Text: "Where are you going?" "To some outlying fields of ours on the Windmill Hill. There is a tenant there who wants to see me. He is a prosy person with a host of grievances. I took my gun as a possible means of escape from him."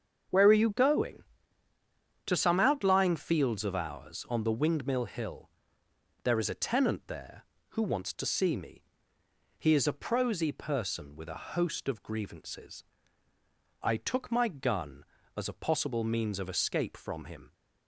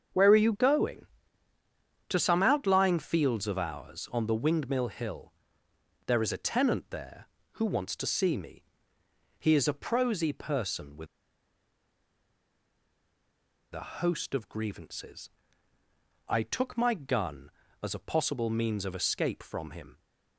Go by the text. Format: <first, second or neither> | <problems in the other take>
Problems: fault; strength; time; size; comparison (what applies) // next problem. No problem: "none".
first | starts louder than the rest; until 2.1 s; 7 dB; also in the first // pauses between "with" and "a"; strong; at 11.0 s; 2.6 s long